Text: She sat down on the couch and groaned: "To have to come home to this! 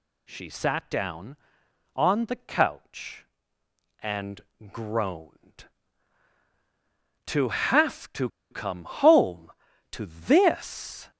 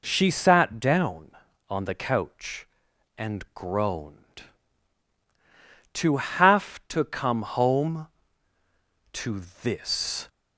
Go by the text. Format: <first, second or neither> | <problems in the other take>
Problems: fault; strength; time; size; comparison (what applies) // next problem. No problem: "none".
second | pauses between "and" and "groaned"; slight; at 4.4 s; 0.32 s long // pauses between "to" and "come"; slight; at 8.2 s; 0.23 s long